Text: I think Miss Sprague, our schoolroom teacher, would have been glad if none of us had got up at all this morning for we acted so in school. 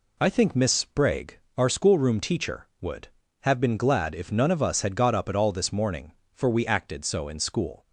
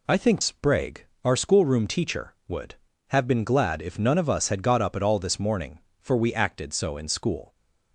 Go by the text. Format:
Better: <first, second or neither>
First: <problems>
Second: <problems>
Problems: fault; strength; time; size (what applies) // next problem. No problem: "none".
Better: first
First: none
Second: skips "Miss"; at 0.4 s